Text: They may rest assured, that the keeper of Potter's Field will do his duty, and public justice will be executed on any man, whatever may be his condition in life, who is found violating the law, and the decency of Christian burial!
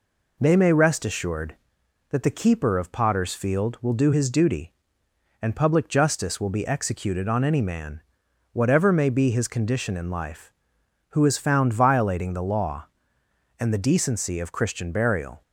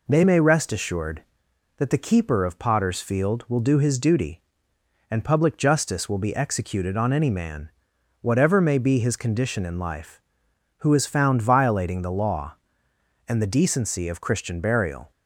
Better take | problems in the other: neither | none

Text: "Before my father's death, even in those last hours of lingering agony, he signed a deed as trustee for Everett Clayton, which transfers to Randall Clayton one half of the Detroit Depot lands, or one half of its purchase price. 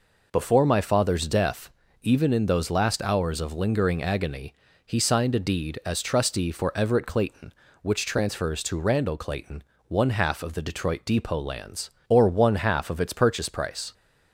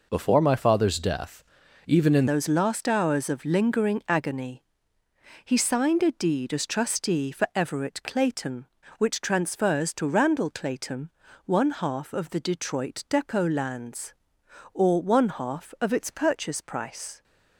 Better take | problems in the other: first | changes voice at "those"; from 2.2 s on; 15.0 s long // pauses between "Clayton" and "one"; at 11.0 s; 0.38 s long; slight in the first

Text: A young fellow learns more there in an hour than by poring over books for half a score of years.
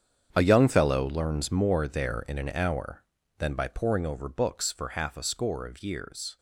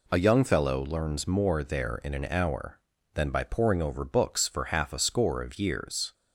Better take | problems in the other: second | gets quieter; strong; throughout; 14 dB

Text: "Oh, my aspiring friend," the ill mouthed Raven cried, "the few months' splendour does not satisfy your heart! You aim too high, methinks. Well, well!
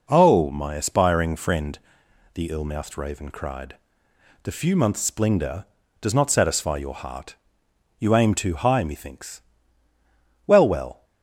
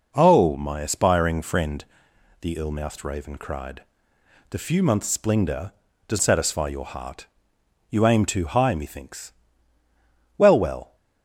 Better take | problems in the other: first | skips "not"; at 6.2 s

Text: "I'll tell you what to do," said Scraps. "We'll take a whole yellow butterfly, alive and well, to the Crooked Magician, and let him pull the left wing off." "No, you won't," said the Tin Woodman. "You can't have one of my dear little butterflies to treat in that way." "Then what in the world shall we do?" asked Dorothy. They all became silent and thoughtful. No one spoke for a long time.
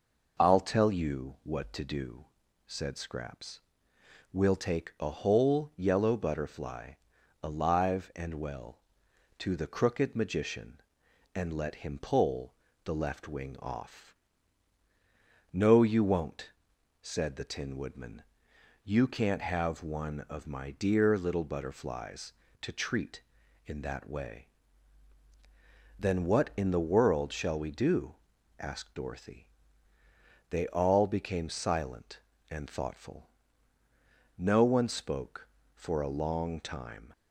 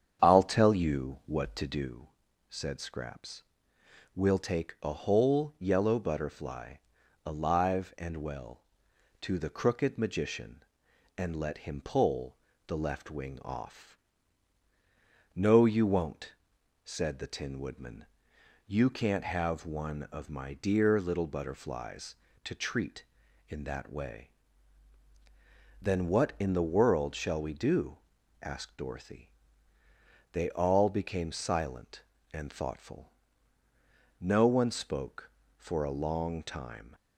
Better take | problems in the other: first | starts louder than the rest; strong; until 1.9 s; 8 dB // pauses between "pull" and "the"; slight; at 12.3 s; 0.30 s long; slight in the first

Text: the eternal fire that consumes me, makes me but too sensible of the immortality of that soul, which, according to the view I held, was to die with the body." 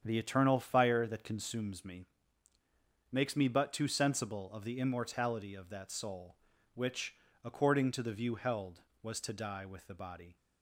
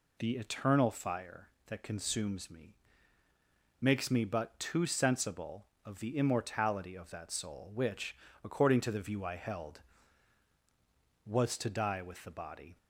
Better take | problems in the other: second | starts louder than the rest; strong; until 1.0 s; 8 dB // skips "I"; at 8.3 s

